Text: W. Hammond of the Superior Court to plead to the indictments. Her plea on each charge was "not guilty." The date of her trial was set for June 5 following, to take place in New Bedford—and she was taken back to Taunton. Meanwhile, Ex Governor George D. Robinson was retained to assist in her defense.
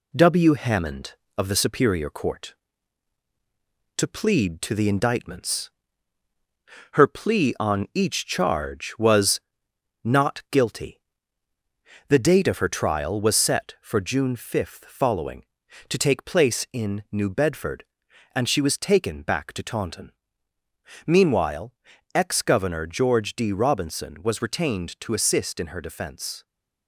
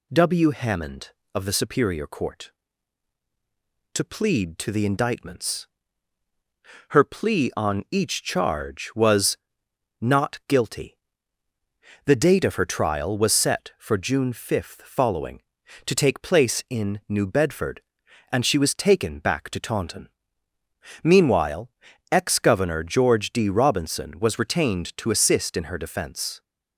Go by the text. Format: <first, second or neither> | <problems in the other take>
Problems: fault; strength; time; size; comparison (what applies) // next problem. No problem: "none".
second | gets quieter; slight; throughout; 3 dB // pauses between "was" and "not"; noticeable; at 9.4 s; 0.64 s long; noticeable in the second